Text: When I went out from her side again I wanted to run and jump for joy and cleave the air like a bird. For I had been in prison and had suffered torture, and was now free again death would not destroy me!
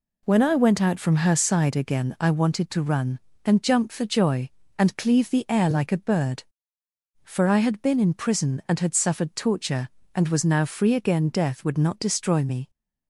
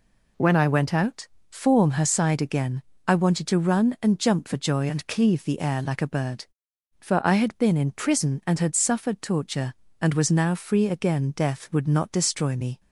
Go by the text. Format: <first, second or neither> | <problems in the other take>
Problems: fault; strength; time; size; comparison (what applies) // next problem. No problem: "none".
first | says "form" for "from"; at 1.4 s // pauses between "again" and "I"; slight; at 2.8 s; 0.24 s long